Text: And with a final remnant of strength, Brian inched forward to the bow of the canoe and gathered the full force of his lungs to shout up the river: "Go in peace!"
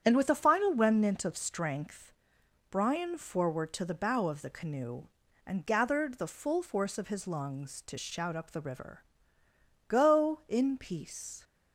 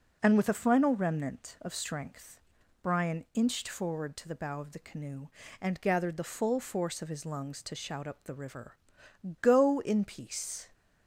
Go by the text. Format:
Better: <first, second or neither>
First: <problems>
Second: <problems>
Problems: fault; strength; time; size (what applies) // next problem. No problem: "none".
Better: second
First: starts louder than the rest; strong; until 1.0 s; 8.5 dB // skips "inched"; at 3.1 s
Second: none